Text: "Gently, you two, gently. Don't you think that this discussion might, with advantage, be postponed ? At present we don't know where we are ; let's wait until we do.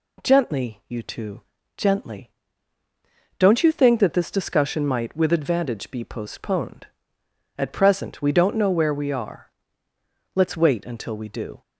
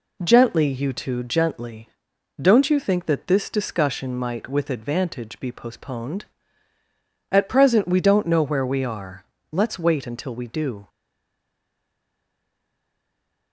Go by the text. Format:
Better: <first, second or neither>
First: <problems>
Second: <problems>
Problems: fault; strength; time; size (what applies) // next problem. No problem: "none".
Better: first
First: none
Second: stays silent after the last word; strong; from 10.8 s on; 2.7 s long